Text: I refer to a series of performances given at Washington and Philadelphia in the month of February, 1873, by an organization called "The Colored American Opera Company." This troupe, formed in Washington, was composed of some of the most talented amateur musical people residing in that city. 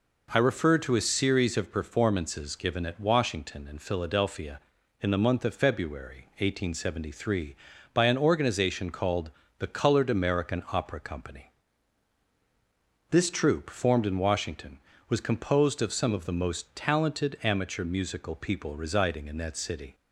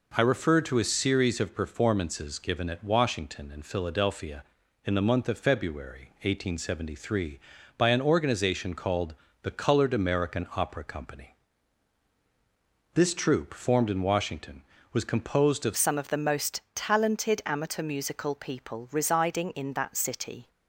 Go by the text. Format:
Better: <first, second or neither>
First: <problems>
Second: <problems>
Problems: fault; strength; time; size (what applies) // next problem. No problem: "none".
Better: first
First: pauses between "called" and "The"; slight; at 9.3 s; 0.26 s long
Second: pauses between "called" and "The"; slight; at 9.1 s; 0.26 s long // changes voice at "some"; from 15.7 s on; 4.8 s long